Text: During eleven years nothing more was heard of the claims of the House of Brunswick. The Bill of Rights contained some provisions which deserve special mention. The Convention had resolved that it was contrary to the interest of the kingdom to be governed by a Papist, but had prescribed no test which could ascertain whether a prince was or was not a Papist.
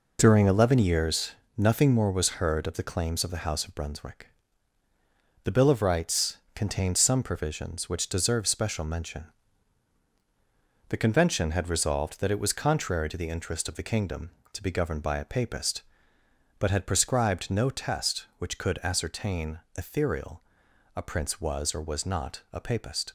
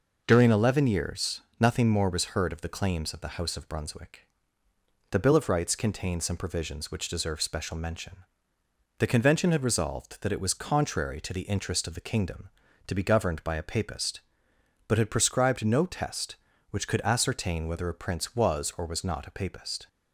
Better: second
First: pauses between "years" and "nothing"; slight; at 1.3 s; 0.24 s long // pauses between "Rights" and "contained"; slight; at 6.3 s; 0.18 s long // says "ethereal" for "whether"; at 19.7 s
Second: pauses between "years" and "nothing"; slight; at 1.4 s; 0.18 s long

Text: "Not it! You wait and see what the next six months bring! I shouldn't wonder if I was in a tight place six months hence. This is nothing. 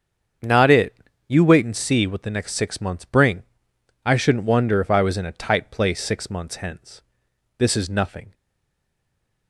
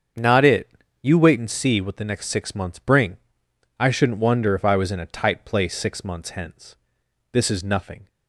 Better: second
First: starts louder than the rest; strong; until 1.7 s; 7 dB // stays silent after the last word; noticeable; from 8.3 s on; 1.1 s long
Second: starts louder than the rest; strong; until 1.4 s; 7 dB

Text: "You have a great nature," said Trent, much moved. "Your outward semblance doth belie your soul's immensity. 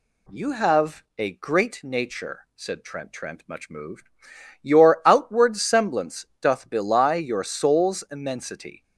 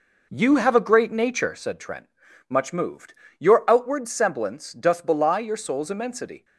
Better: second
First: says "Trent" twice; at 3.1 s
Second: none

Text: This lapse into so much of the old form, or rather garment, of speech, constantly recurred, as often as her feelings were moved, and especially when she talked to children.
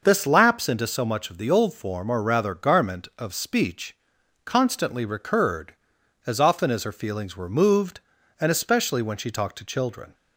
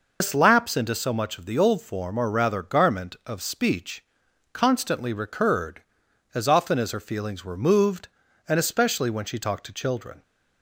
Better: first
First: none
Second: loses the start of "This"; at 0.2 s; 85 ms

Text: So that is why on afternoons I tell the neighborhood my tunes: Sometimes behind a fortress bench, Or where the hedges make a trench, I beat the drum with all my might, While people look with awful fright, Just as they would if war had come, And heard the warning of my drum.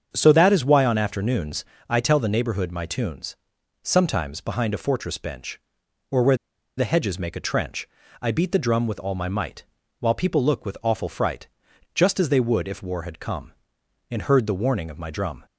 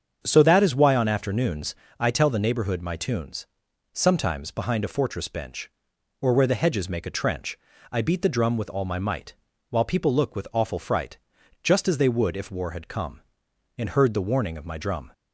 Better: second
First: starts louder than the rest; strong; until 1.1 s; 7 dB // pauses between "afternoons" and "I"; slight; at 1.6 s; 0.26 s long // pauses between "where" and "the"; at 6.3 s; 0.42 s long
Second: starts louder than the rest; strong; until 1.2 s; 7 dB // pauses between "afternoons" and "I"; slight; at 1.7 s; 0.26 s long

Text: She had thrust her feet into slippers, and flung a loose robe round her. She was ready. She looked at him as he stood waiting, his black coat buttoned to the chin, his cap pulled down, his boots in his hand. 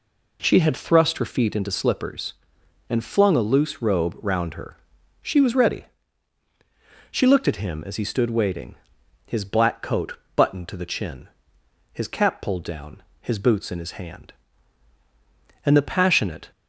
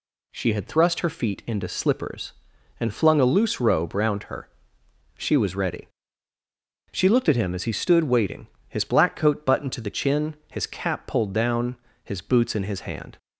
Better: second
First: pauses between "coat" and "buttoned"; slight; at 10.1 s; 0.18 s long // goes on to say "And the passionate"; noticeable; from 15.6 s on; 0.88 s long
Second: none

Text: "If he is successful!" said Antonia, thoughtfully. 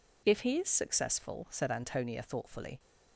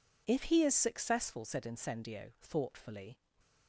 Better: first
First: none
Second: says "Incendio" for "Antonia"; at 1.6 s

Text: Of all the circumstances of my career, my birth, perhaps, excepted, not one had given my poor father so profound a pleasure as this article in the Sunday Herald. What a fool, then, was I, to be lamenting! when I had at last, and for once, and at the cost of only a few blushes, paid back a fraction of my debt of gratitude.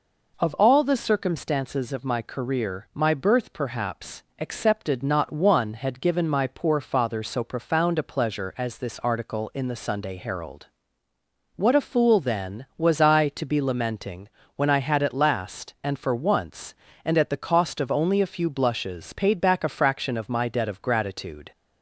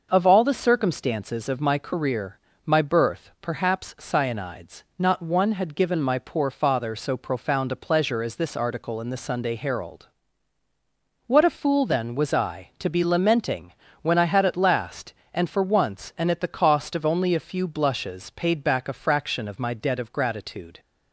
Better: first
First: none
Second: says "cyanides" for "excepted"; at 3.9 s

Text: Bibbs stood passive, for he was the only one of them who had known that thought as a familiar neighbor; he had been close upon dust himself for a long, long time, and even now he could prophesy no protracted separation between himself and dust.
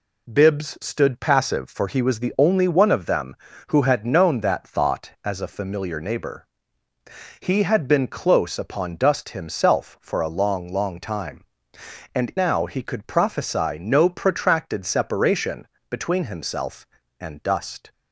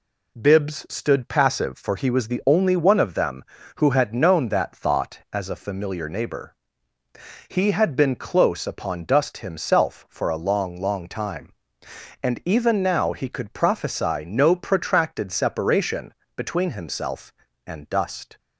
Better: second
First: skips "even"; at 12.3 s // pauses between "separation" and "between"; slight; at 15.6 s; 0.22 s long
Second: pauses between "separation" and "between"; slight; at 16.1 s; 0.22 s long

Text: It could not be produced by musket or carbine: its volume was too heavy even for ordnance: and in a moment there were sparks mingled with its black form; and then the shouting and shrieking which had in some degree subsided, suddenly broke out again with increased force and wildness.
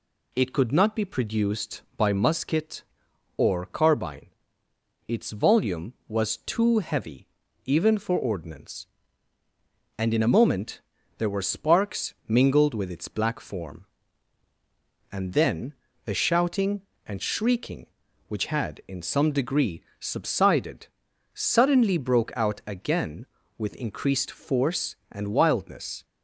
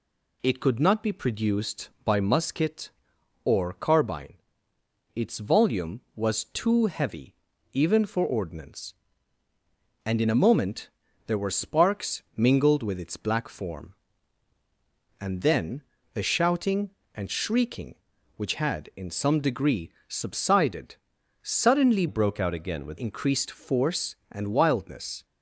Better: first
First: pauses between "heavy" and "even"; at 7.2 s; 0.40 s long // pauses between "moment" and "there"; at 10.7 s; 0.38 s long // pauses between "sparks" and "mingled"; slight; at 12.1 s; 0.16 s long // pauses between "then" and "the"; slight; at 15.7 s; 0.32 s long // pauses between "degree" and "subsided"; slight; at 19.8 s; 0.18 s long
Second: pauses between "heavy" and "even"; at 7.3 s; 0.40 s long // pauses between "moment" and "there"; at 10.8 s; 0.38 s long // pauses between "sparks" and "mingled"; slight; at 12.2 s; 0.16 s long // pauses between "then" and "the"; slight; at 15.8 s; 0.32 s long // pauses between "degree" and "subsided"; slight; at 19.8 s; 0.18 s long // changes voice from "broke" to "with"; from 22.0 to 22.9 s; 0.9 s long

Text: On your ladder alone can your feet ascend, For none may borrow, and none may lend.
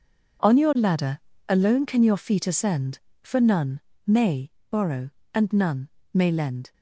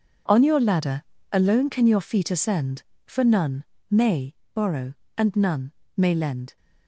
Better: neither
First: pauses between "ladder" and "alone"; slight; at 1.1 s; 0.28 s long // pauses between "none" and "may"; slight; at 3.7 s; 0.26 s long // pauses between "may" and "borrow"; slight; at 4.5 s; 0.20 s long // pauses between "none" and "may"; slight; at 5.8 s; 0.26 s long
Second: pauses between "ladder" and "alone"; slight; at 1.0 s; 0.28 s long // pauses between "none" and "may"; slight; at 3.6 s; 0.26 s long // pauses between "may" and "borrow"; slight; at 4.3 s; 0.20 s long // pauses between "none" and "may"; slight; at 5.6 s; 0.26 s long

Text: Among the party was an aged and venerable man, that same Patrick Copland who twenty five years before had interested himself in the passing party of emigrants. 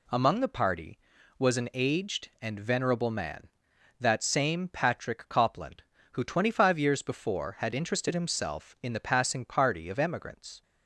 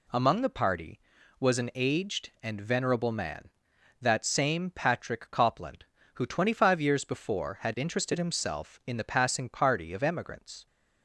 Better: neither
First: none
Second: none

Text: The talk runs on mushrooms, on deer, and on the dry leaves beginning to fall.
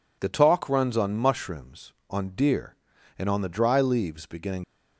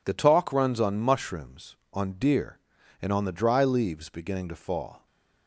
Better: second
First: stops before "to fall"; at 4.6 s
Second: none

